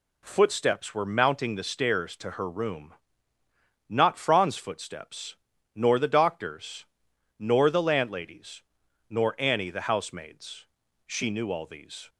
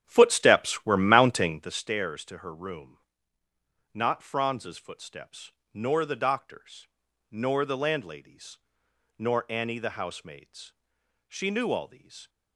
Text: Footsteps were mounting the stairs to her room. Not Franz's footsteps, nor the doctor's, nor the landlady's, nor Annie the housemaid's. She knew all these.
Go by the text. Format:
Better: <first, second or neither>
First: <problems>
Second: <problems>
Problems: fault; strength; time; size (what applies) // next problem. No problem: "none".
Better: first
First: none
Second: starts louder than the rest; strong; until 1.8 s; 9 dB